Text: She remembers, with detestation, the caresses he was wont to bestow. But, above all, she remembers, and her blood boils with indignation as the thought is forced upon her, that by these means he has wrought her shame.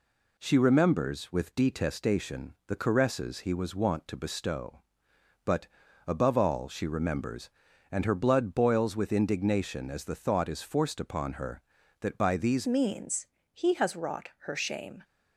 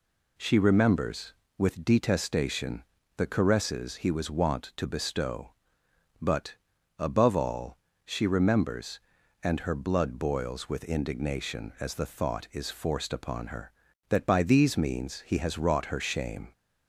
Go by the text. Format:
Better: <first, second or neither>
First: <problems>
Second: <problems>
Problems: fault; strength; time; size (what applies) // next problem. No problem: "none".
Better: second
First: changes voice at "means"; from 12.6 s on; 2.4 s long // pauses between "means" and "he"; slight; at 13.2 s; 0.24 s long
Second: none